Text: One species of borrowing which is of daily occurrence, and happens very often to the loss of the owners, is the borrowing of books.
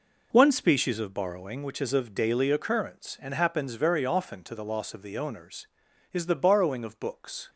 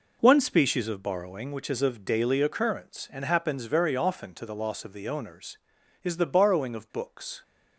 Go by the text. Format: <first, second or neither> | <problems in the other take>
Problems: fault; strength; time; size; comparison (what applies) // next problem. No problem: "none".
neither | none